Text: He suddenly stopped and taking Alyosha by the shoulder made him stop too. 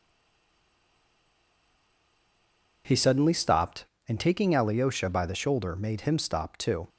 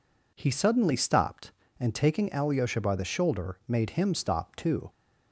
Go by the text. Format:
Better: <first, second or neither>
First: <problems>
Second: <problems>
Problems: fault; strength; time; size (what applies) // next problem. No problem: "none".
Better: second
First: stays silent before the first word; strong; until 2.8 s; 2.8 s long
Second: none